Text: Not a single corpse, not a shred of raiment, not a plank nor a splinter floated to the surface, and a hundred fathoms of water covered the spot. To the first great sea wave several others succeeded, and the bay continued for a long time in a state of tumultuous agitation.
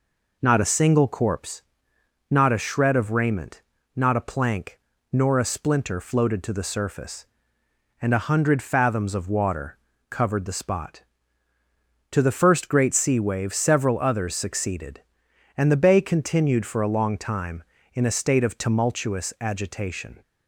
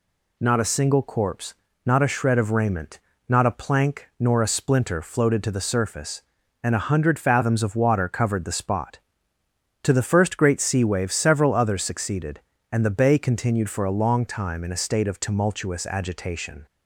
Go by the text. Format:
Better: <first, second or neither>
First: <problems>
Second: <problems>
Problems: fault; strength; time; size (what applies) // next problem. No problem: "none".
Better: second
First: starts louder than the rest; noticeable; until 1.5 s; 4.5 dB // pauses between "plank" and "nor"; slight; at 4.7 s; 0.32 s long // pauses between "water" and "covered"; slight; at 9.7 s; 0.32 s long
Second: none